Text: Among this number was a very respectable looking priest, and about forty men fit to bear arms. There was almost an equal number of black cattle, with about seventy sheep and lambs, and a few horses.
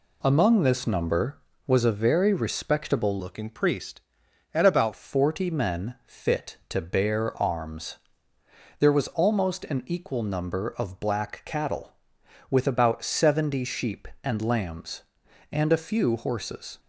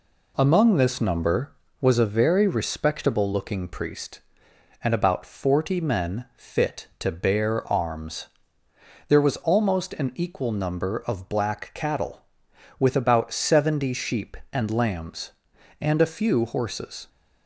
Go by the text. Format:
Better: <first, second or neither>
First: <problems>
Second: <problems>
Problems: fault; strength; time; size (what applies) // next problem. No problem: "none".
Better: second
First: changes voice from "looking" to "about"; from 3.1 to 4.9 s; 1.8 s long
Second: none